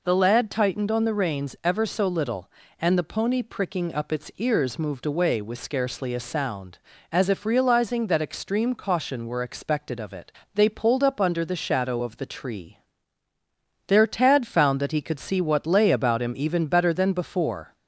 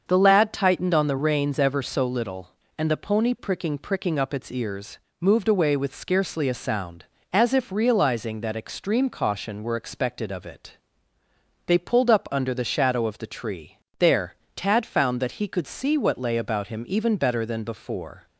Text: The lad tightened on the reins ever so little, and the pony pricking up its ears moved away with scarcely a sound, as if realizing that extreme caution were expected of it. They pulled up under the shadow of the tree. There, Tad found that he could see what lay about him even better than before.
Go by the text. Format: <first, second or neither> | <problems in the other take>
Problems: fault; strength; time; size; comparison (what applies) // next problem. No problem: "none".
first | starts louder than the rest; until 1.0 s; 6.5 dB // says "pricking" twice; at 3.7 s // pauses between "ears" and "moved"; slight; at 4.9 s; 0.22 s long